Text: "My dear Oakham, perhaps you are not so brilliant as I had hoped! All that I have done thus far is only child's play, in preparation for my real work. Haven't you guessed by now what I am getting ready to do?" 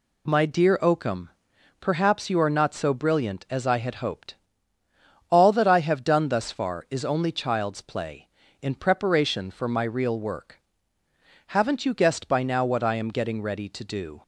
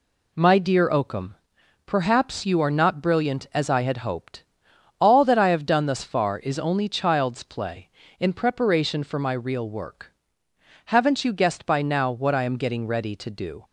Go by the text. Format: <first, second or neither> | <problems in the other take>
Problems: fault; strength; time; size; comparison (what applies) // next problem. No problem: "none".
first | skips "so"; at 3.0 s